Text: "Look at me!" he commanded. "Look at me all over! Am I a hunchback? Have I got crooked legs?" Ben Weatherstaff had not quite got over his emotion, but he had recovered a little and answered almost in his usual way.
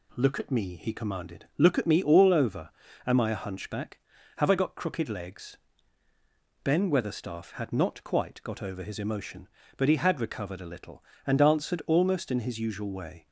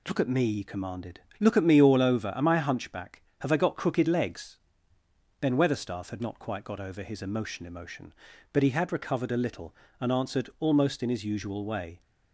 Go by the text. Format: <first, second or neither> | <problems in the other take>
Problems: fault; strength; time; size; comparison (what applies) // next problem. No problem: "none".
first | says "emotion" twice; at 7.6 s